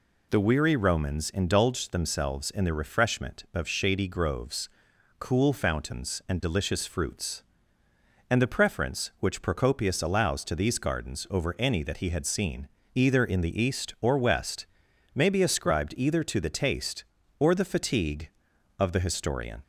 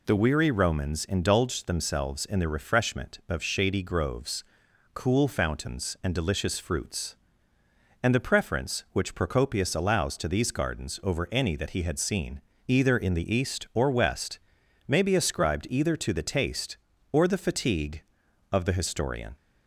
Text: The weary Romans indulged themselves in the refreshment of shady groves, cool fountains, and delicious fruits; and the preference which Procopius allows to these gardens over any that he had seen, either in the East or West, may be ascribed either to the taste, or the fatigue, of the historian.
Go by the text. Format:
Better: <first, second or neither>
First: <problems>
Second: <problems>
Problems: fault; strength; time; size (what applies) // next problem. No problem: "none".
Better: neither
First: none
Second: none